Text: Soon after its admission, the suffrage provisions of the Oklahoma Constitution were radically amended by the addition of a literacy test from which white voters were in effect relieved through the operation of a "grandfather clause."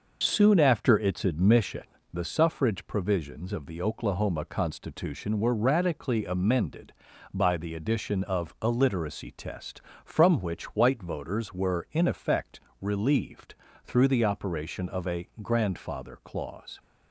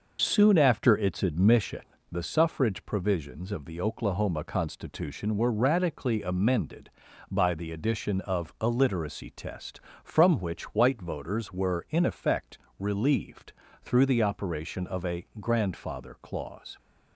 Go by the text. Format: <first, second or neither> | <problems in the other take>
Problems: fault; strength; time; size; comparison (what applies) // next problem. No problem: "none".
neither | pauses between "effect" and "relieved"; slight; the same in both // pauses between "relieved" and "through"; slight; the same in both